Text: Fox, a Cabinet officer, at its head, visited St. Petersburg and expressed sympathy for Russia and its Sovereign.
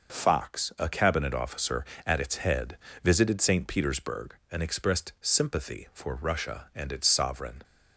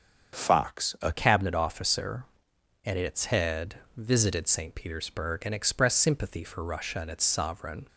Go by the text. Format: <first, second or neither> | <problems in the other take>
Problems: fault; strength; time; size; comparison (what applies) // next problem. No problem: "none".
first | starts louder than the rest; strong; until 1.3 s; 7 dB // changes voice at "Cabinet"; from 1.1 s on; 6.7 s long